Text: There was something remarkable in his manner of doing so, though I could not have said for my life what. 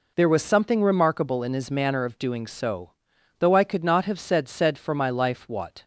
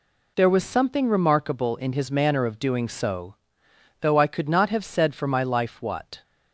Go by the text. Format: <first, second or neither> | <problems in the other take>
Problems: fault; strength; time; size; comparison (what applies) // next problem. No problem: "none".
second | says "said" twice; at 4.4 s